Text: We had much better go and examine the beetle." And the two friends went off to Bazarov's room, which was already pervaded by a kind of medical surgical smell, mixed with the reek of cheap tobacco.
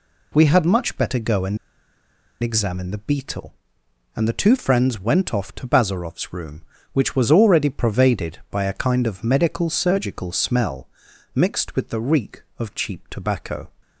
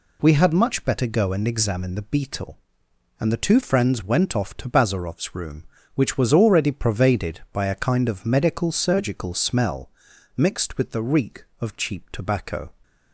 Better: second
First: pauses between "and" and "examine"; noticeable; at 1.5 s; 0.85 s long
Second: none

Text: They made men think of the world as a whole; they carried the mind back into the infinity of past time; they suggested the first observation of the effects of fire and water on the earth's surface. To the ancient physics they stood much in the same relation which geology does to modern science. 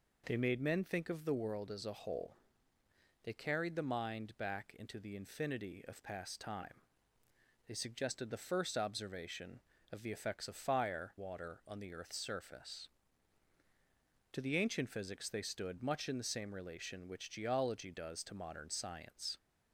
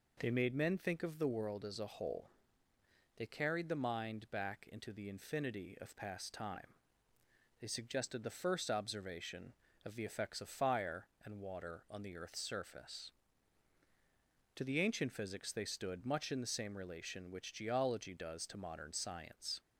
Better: second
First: skips "and"; at 11.1 s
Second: none

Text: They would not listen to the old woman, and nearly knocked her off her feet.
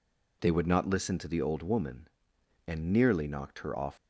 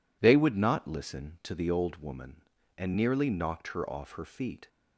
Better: second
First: stops before "her feet"; at 3.9 s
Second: none

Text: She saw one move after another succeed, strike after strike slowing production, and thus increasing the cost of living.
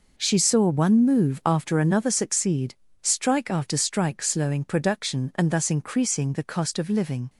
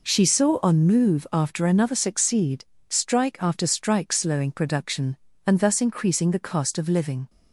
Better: first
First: none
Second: says "on" for "one"; at 0.6 s

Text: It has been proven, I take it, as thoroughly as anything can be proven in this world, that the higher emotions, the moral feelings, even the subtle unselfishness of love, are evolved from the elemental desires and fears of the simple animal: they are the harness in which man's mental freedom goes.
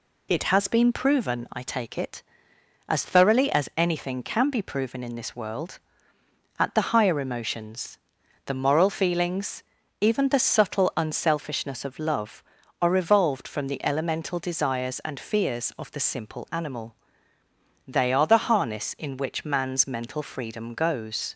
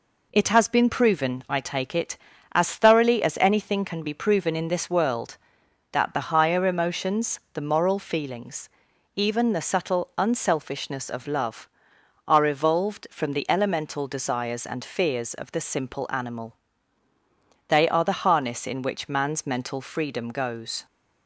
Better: second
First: says "at" for "that"; at 6.5 s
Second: none

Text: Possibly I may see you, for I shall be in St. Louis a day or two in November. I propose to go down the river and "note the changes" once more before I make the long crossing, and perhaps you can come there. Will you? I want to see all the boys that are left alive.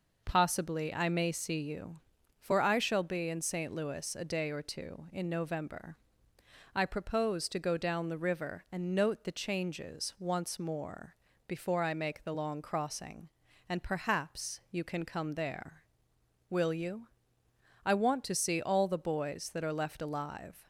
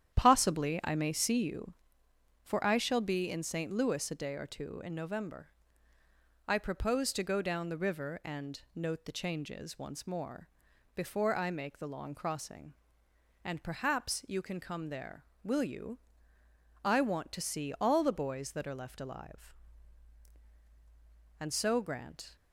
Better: first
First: pauses between "more" and "before"; slight; at 11.1 s; 0.32 s long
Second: starts louder than the rest; strong; until 1.2 s; 10 dB // pauses between "and" and "note"; slight; at 8.5 s; 0.16 s long // pauses between "more" and "before"; noticeable; at 10.4 s; 0.46 s long // goes on to say "And so Grant"; noticeable; from 21.3 s on; 0.96 s long

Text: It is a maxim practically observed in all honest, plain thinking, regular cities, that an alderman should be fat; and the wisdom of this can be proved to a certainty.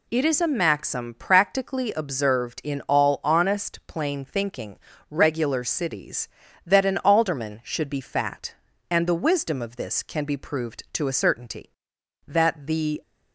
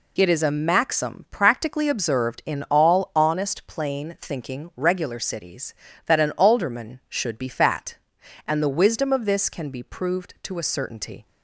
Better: second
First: goes on to say "That the"; noticeable; from 12.2 s on; 0.76 s long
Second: none

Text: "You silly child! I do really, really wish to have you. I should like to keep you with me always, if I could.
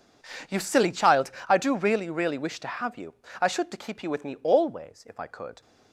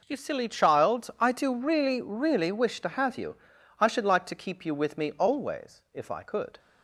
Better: second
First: skips "like"; at 3.7 s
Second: none

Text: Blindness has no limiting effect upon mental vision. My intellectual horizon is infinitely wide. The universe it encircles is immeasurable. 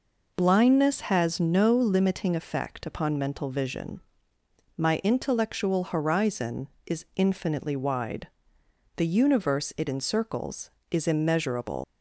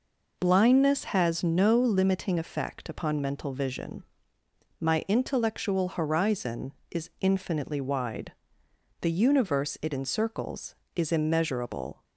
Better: second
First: leaves "immeasurable" unfinished; at 11.8 s; 150 ms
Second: none

